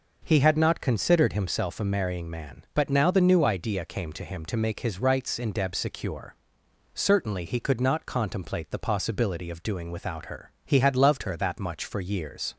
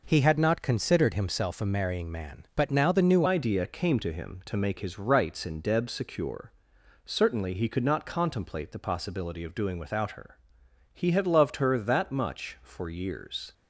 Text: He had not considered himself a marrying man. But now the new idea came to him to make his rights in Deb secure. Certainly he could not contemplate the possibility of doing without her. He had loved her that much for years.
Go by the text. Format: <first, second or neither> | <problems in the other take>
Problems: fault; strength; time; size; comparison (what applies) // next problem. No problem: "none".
first | changes voice at "idea"; from 3.2 s on; 10.3 s long